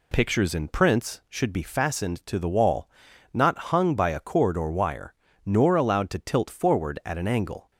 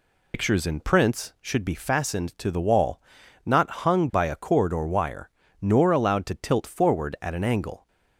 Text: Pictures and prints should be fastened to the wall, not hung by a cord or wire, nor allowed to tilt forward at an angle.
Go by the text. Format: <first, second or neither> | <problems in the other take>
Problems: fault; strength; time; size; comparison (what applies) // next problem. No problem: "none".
first | loses the start of "Pictures"; at 0.3 s; 110 ms